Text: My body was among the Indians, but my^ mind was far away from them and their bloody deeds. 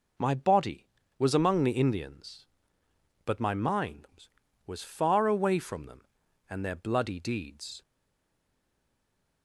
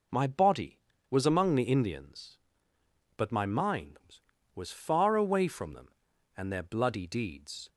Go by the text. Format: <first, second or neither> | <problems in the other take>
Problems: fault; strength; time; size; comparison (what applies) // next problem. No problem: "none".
second | stays silent after the last word; noticeable; from 7.8 s on; 1.6 s long